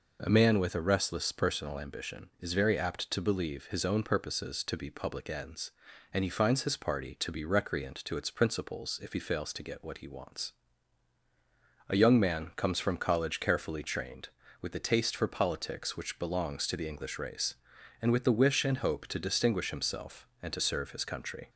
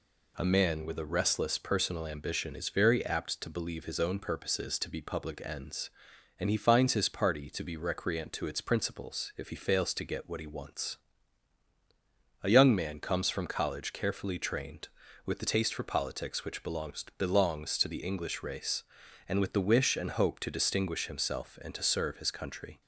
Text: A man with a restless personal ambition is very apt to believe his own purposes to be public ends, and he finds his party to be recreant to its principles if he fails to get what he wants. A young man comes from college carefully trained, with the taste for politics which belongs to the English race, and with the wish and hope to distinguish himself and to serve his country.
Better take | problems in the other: first | says "belongs" twice; at 17.1 s

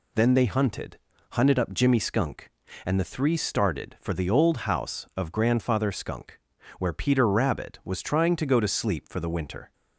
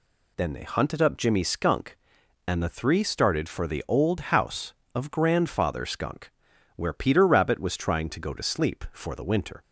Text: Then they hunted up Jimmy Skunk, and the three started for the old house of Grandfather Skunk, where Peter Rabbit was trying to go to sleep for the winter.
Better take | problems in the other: second | says "hunted" twice; at 1.3 s

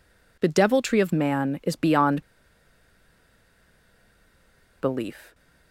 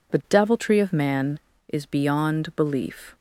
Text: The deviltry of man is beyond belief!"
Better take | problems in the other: second | pauses between "beyond" and "belief"; strong; at 2.2 s; 2.5 s long

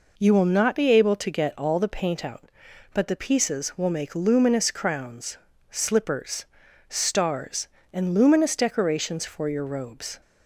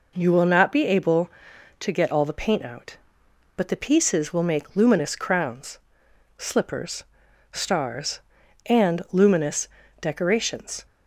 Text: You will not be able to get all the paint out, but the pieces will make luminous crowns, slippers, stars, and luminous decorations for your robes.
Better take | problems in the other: first | pauses between "luminous" and "decorations"; slight; at 9.6 s; 0.32 s long // stops before "for your robes"; at 10.8 s

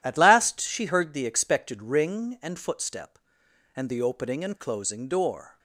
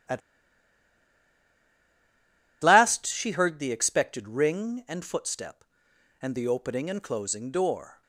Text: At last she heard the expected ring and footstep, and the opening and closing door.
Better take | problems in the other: first | pauses between "At" and "last"; strong; at 0.2 s; 2.4 s long

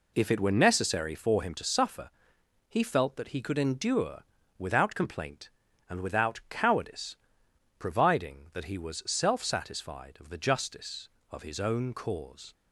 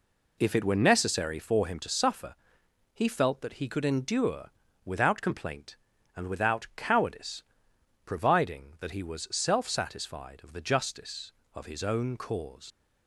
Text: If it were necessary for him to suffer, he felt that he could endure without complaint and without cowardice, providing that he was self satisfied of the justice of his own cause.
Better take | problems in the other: first | pauses between "endure" and "without"; slight; at 4.4 s; 0.34 s long; slight in the first // leaves "cause" unfinished; at 12.7 s; 65 ms

